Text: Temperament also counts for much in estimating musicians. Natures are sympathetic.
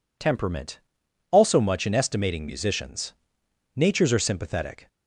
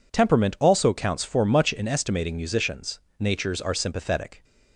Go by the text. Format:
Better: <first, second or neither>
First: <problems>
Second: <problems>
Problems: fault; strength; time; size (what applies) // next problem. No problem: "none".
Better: second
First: pauses between "Temperament" and "also"; noticeable; at 0.7 s; 0.52 s long // skips "counts for"; at 1.5 s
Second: none